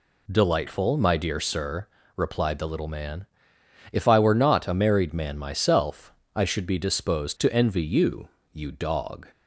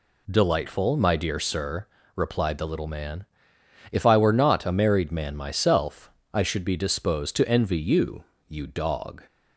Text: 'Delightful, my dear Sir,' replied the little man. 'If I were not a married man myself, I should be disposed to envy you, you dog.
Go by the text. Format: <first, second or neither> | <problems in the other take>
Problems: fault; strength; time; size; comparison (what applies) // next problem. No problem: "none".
neither | none